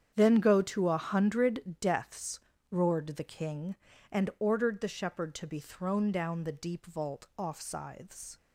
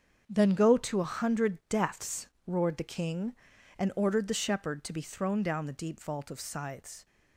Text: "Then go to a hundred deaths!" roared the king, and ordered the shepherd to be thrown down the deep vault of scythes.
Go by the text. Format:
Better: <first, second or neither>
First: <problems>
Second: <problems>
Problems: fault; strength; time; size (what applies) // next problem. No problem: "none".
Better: second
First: starts louder than the rest; strong; until 1.1 s; 8.5 dB // says "off" for "of"; at 7.3 s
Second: starts louder than the rest; until 1.2 s; 7 dB